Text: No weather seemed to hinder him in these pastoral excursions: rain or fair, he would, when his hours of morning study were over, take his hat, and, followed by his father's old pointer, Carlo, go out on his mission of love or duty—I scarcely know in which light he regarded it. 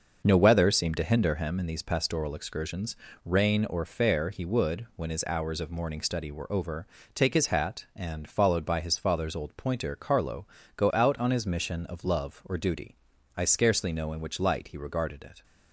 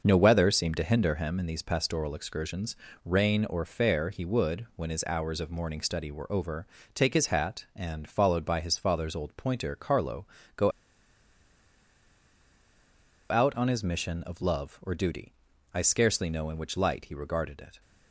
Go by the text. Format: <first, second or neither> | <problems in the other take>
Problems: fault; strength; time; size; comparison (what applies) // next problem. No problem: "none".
first | starts louder than the rest; until 1.0 s; 6 dB; also in the first // pauses between "go" and "out"; strong; at 10.7 s; 2.5 s long